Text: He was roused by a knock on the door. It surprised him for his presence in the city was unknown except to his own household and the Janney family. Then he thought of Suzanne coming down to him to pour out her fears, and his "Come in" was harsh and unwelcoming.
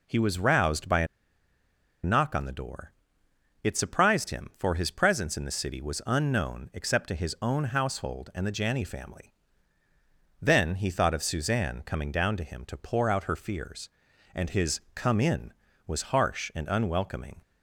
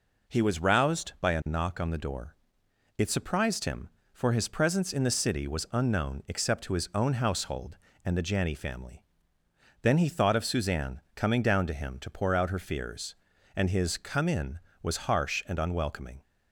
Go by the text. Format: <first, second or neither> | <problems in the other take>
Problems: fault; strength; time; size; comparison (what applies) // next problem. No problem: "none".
second | pauses between "a" and "knock"; noticeable; at 1.0 s; 0.97 s long // pauses between "his" and "Come"; slight; at 14.7 s; 0.16 s long